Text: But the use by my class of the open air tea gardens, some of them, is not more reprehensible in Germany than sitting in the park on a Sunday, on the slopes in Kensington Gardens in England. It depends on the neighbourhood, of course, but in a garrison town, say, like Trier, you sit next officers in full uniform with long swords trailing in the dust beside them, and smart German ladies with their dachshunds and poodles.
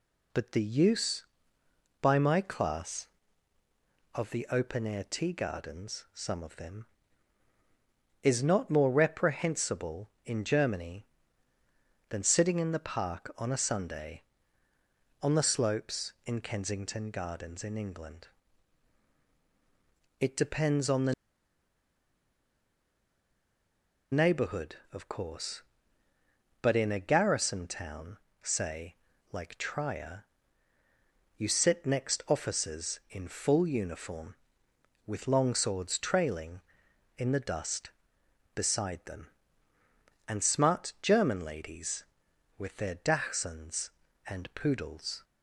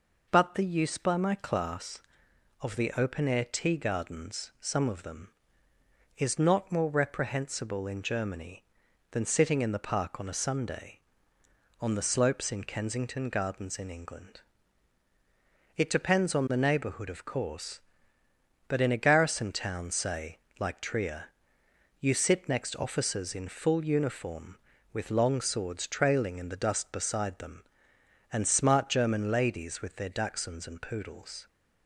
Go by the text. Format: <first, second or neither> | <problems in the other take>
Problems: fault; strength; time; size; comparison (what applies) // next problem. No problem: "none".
second | pauses between "the" and "neighbourhood"; strong; at 21.1 s; 2.9 s long